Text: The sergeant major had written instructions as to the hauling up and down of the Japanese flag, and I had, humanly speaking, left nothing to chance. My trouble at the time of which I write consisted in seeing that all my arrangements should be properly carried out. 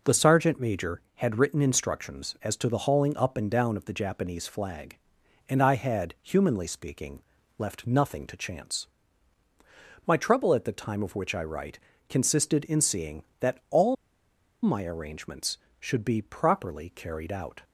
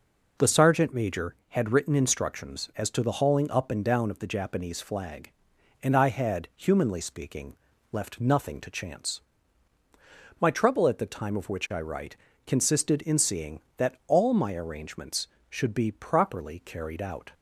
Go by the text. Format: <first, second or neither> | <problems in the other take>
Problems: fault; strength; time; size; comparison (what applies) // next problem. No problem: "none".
second | pauses between "write" and "consisted"; slight; at 11.7 s; 0.32 s long; slight in the second // pauses between "all" and "my"; noticeable; at 13.9 s; 0.68 s long